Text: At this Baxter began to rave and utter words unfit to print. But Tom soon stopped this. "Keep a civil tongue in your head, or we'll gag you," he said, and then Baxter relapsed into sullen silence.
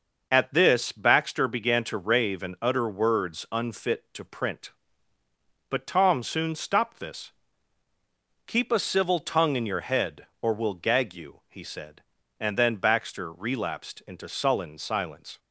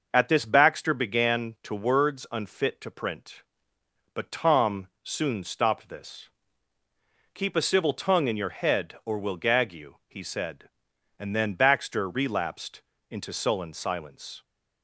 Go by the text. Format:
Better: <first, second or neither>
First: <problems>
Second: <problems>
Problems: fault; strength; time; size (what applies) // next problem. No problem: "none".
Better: first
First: none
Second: skips "rave and utter"; at 1.7 s // pauses between "Tom" and "soon"; slight; at 4.8 s; 0.16 s long // pauses between "relapsed" and "into"; slight; at 12.8 s; 0.28 s long